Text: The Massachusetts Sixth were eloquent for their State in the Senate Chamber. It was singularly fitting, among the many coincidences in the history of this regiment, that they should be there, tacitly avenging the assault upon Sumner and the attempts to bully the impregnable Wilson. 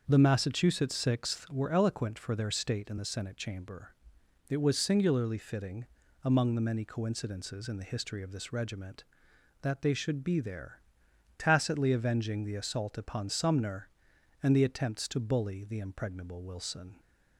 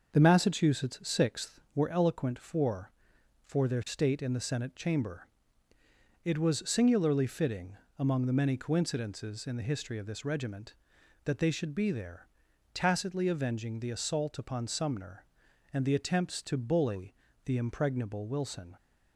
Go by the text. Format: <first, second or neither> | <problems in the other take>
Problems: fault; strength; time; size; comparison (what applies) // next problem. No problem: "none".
first | starts louder than the rest; until 1.1 s; 6.5 dB; also in the first // says "for" twice; at 3.4 s // pauses between "bully" and "the"; slight; at 17.1 s; 0.30 s long